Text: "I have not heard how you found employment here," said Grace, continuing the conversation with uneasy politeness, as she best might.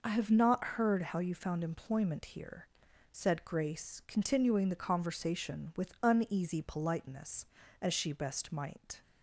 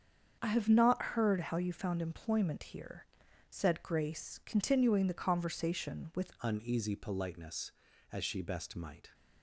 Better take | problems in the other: first | starts louder than the rest; until 1.4 s; 7 dB // changes voice at "uneasy"; from 6.4 s on; 2.7 s long

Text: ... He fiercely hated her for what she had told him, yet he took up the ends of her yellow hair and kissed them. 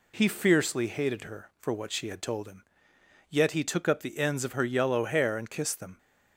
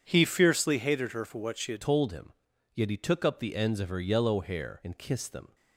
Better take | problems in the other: first | starts louder than the rest; strong; until 1.0 s; 8 dB // changes voice at "told"; from 1.8 s on; 3.7 s long

